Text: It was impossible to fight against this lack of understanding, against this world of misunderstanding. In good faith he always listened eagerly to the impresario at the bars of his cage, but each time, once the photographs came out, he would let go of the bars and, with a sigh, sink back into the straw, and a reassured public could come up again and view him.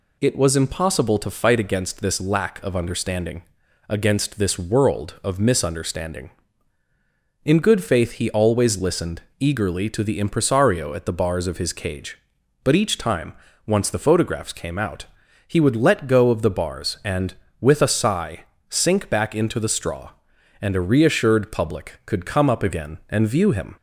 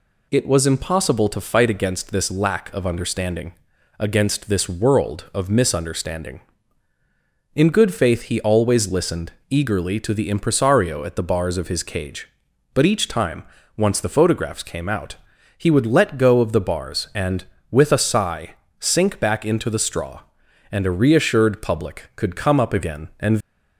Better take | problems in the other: first | pauses between "listened" and "eagerly"; slight; at 9.3 s; 0.16 s long; slight in the first // stops before "view him"; at 23.4 s

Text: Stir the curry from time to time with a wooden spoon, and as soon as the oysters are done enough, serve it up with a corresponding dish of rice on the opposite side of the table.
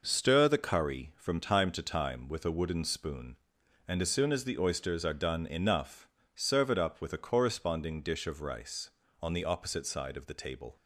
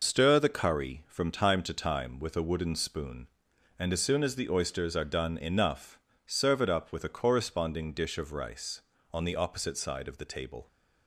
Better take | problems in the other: first | loses the start of "Stir"; at 0.0 s; 75 ms

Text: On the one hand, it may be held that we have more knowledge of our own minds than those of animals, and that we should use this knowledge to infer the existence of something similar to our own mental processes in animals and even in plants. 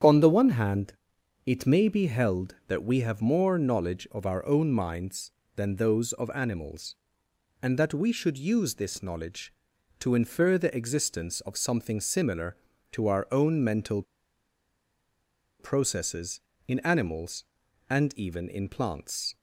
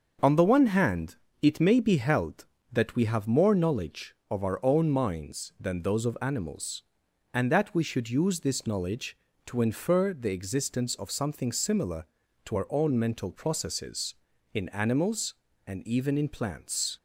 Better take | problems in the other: second | starts louder than the rest; strong; until 1.5 s; 8.5 dB; also in the second // pauses between "mental" and "processes"; strong; at 14.0 s; 1.5 s long

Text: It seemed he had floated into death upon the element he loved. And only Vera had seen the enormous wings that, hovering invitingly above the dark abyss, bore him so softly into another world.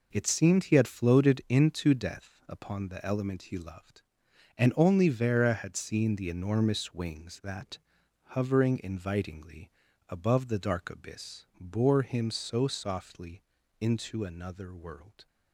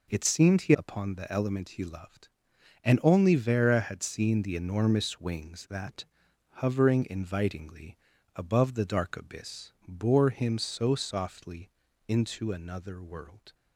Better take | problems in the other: first | skips "had floated into death"; at 0.7 s // pauses between "invitingly" and "above"; at 7.9 s; 0.40 s long; also in the first // pauses between "softly" and "into"; slight; at 11.6 s; 0.36 s long; slight in the first

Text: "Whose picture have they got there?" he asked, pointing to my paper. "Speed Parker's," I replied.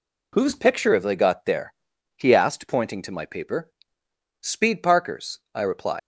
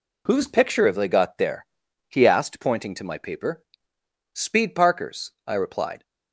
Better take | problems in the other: second | leaves "replied" unfinished; at 5.9 s; 105 ms

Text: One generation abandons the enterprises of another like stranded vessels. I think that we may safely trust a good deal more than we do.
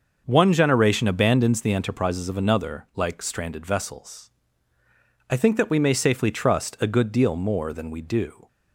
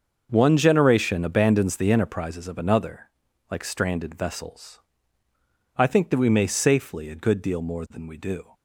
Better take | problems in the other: first | starts louder than the rest; until 1.3 s; 6.5 dB; also in the first // pauses between "another" and "like"; at 3.1 s; 0.40 s long // skips "trust"; at 7.0 s

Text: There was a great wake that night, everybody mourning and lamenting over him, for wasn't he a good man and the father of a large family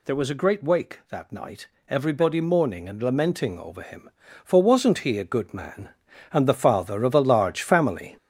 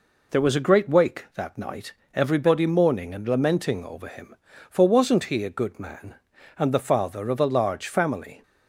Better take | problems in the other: second | gets louder; throughout; 6.5 dB

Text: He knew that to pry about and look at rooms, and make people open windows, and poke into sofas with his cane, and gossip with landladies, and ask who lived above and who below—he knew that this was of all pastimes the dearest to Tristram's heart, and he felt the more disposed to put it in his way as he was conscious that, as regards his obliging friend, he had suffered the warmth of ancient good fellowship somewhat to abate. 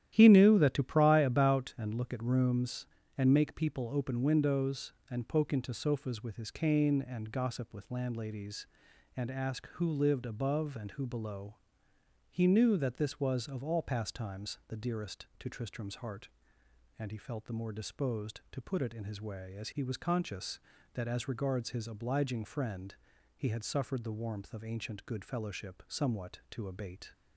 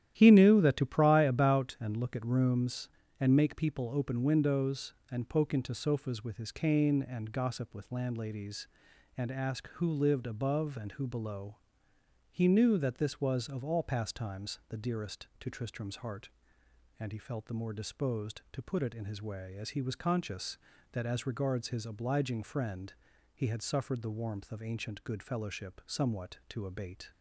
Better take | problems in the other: neither | starts louder than the rest; strong; the same in both

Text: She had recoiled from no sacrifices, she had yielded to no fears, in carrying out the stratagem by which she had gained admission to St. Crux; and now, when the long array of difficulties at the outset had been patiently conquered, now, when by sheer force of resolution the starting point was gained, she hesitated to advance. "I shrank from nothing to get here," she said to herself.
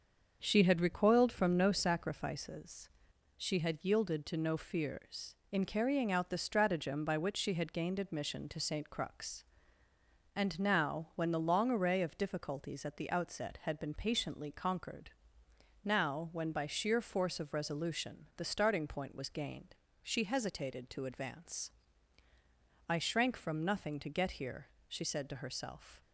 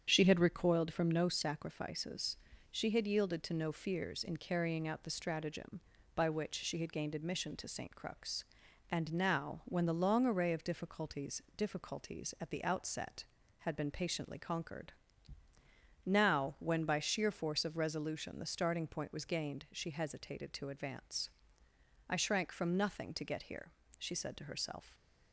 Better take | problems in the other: first | starts louder than the rest; strong; until 1.0 s; 8 dB; also in the first // says "difficulties" twice; at 11.5 s

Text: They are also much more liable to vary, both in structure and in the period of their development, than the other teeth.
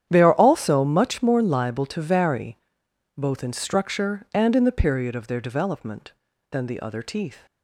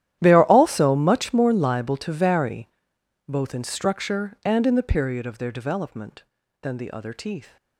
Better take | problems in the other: first | gets quieter; strong; throughout; 20 dB // starts louder than the rest; strong; until 1.2 s; 12 dB; strong in the first

